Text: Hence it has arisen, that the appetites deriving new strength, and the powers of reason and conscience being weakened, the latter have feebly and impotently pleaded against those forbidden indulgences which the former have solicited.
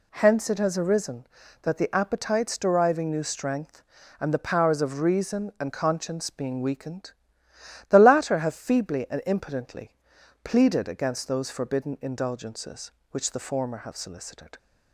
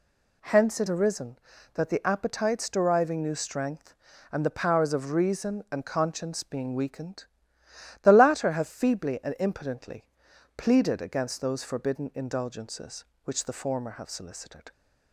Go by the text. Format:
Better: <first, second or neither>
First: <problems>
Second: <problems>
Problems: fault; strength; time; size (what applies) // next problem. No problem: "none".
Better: first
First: pauses between "impotently" and "pleaded"; noticeable; at 9.9 s; 0.52 s long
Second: skips "has"; at 0.8 s // pauses between "impotently" and "pleaded"; noticeable; at 10.0 s; 0.52 s long